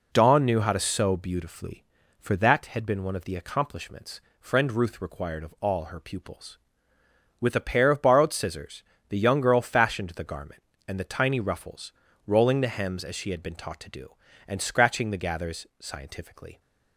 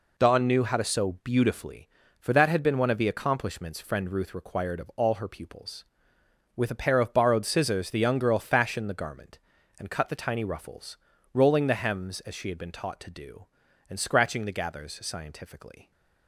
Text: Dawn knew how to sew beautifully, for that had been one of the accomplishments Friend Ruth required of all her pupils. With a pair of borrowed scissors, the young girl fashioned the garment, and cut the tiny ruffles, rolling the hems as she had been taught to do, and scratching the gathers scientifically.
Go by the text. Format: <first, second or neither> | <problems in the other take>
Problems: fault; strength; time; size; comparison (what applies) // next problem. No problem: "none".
second | pauses between "accomplishments" and "Friend"; slight; at 4.1 s; 0.20 s long // skips "cut"; at 10.9 s